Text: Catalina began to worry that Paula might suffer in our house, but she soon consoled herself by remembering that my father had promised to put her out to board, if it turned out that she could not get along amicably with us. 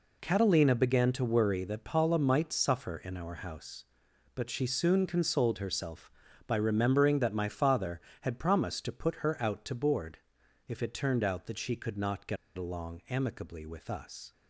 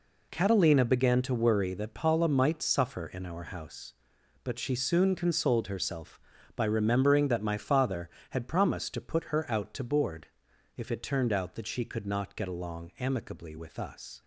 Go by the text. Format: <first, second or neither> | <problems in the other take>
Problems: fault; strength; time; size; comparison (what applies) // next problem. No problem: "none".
second | pauses between "get" and "along"; slight; at 12.3 s; 0.21 s long